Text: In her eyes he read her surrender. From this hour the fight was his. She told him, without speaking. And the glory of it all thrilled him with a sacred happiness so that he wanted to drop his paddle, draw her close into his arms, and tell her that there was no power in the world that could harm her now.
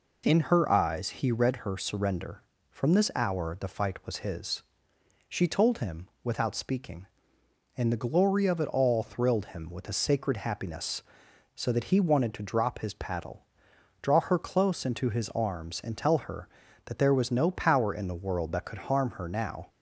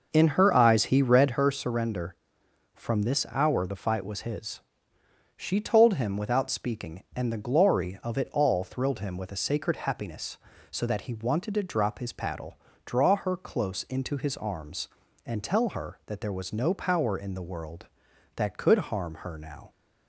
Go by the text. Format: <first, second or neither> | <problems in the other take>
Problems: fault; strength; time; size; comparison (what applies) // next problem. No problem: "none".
first | starts louder than the rest; noticeable; until 1.5 s; 5.5 dB